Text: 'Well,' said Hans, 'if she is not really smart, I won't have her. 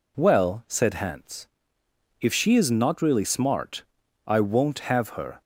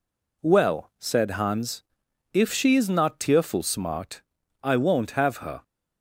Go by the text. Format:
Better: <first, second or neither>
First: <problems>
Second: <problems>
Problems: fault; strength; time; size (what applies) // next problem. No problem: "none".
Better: first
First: none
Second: says "tearful" for "really"; at 3.1 s